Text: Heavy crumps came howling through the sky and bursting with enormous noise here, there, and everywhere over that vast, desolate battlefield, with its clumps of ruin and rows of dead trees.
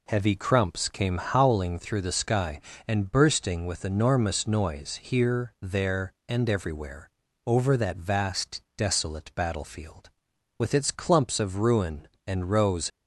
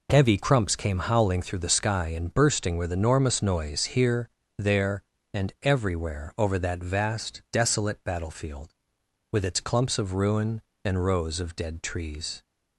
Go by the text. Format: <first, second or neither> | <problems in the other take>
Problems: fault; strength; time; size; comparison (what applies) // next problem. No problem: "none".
second | pauses between "everywhere" and "over"; slight; at 7.1 s; 0.34 s long // stops before "of dead trees"; at 12.9 s